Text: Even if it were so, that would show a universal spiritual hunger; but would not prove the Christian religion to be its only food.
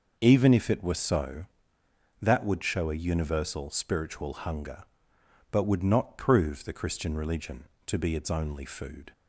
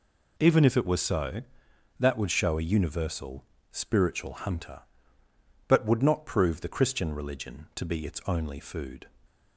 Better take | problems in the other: first | pauses between "universal" and "spiritual"; slight; at 3.4 s; 0.26 s long // says "hunter" for "hunger"; at 4.3 s

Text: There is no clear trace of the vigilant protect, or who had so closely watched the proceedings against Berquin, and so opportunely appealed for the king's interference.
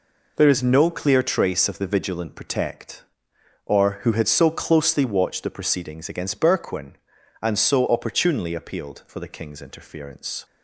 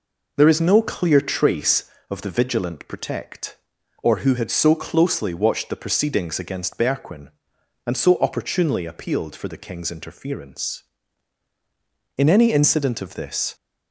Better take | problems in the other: first | goes on to say "In any incident of this"; from 12.1 s on; 1.3 s long

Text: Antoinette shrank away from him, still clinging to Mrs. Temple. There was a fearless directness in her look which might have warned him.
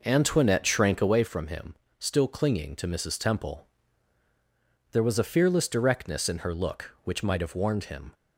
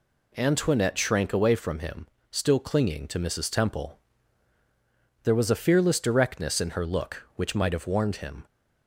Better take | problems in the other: second | starts louder than the rest; noticeable; until 1.1 s; 5.5 dB

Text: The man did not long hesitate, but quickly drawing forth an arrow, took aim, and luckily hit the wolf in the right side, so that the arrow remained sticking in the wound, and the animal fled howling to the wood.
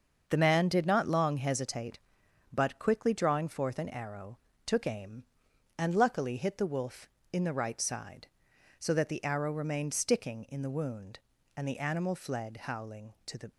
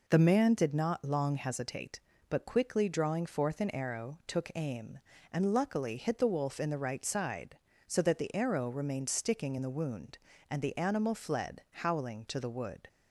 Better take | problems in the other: second | starts louder than the rest; until 1.2 s; 6.5 dB // stops before "wood"; at 13.5 s

